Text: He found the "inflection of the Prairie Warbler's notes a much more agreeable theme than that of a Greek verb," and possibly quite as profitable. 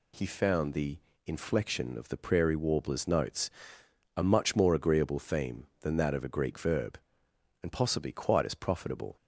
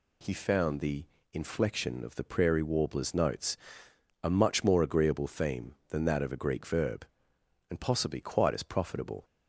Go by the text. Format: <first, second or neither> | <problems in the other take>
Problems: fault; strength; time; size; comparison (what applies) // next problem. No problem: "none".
neither | pauses between "the" and "inflection"; slight; the same in both // pauses between "notes" and "a"; noticeable; the same in both